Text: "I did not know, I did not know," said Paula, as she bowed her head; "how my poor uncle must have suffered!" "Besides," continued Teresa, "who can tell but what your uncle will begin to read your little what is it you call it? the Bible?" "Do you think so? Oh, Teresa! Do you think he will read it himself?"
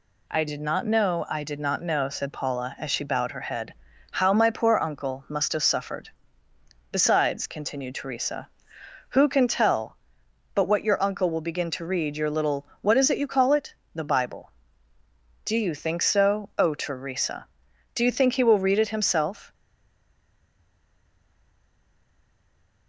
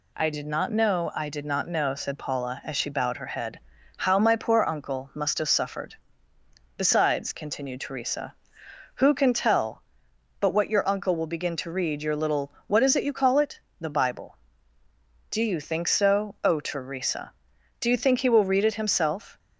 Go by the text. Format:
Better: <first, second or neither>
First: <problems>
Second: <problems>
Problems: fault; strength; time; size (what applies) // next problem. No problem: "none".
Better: second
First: stays silent after the last word; strong; from 19.5 s on; 3.3 s long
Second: none